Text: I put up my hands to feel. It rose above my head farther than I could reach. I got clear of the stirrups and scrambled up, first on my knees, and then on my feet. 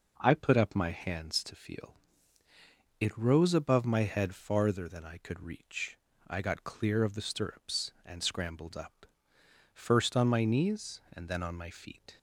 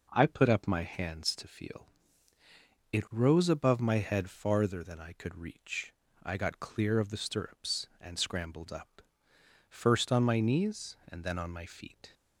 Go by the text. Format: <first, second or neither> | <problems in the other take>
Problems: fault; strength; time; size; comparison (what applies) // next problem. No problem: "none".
neither | none